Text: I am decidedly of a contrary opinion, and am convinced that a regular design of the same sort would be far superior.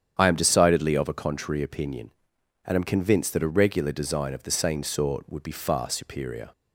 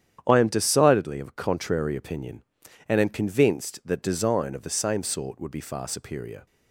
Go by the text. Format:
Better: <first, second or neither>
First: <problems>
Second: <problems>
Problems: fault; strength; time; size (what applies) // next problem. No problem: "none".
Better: first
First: starts louder than the rest; strong; until 1.1 s; 8.5 dB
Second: starts louder than the rest; strong; until 1.2 s; 9 dB // skips "a regular"; at 4.0 s